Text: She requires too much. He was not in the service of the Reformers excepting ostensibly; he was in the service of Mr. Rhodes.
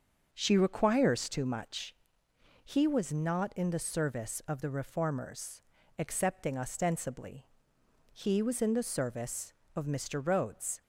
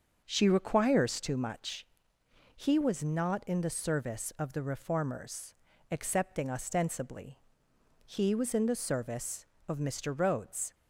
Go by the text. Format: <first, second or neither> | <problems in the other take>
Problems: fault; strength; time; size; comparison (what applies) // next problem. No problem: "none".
neither | starts louder than the rest; the same in both // pauses between "Reformers" and "excepting"; the same in both